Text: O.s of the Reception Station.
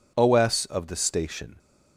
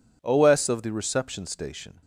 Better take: second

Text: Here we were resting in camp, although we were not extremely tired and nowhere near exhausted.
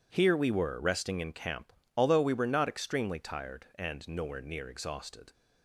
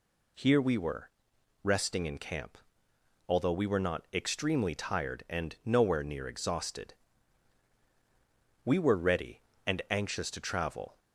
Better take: first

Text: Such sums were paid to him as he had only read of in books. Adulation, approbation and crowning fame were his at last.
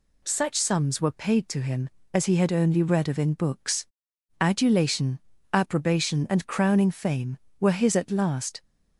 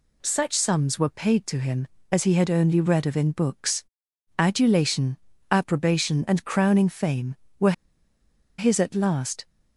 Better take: first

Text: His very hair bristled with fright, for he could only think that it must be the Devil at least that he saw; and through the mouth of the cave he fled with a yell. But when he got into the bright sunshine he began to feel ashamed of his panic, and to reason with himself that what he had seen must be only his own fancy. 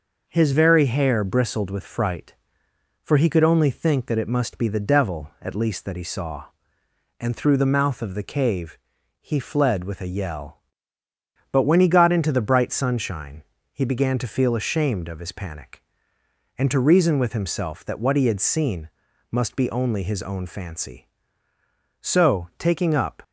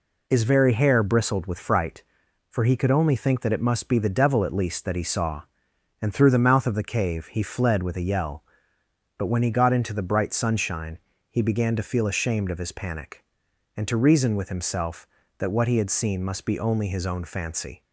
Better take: second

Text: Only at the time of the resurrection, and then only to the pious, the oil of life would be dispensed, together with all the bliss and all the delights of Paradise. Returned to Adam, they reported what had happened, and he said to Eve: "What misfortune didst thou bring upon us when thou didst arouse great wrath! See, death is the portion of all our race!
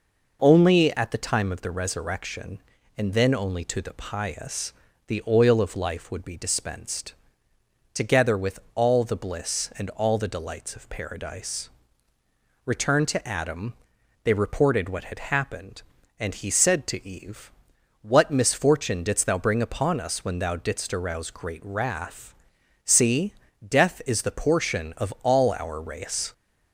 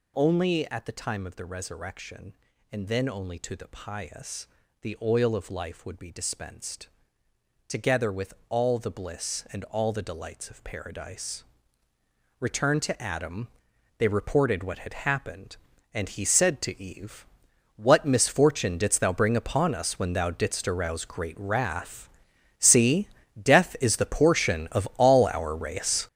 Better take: first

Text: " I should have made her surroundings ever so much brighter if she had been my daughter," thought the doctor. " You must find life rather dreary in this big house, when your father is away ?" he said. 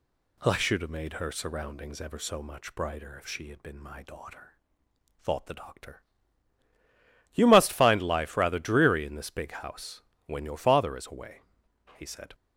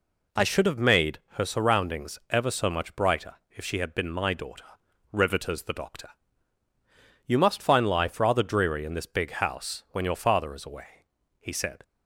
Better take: first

